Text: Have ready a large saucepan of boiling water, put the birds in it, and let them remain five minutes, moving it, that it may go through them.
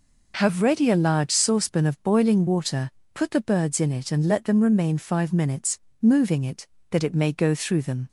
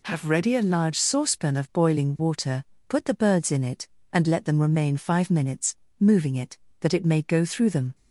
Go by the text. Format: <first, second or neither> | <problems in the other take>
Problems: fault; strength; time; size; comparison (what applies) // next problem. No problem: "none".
neither | none